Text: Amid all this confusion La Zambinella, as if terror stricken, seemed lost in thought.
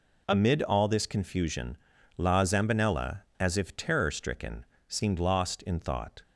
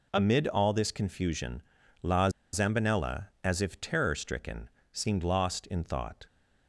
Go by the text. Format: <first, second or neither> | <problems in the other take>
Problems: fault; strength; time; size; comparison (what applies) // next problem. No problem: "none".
first | pauses between "confusion" and "La"; at 1.6 s; 0.40 s long; also in the first // pauses between "La" and "Zambinella"; slight; at 2.2 s; 0.24 s long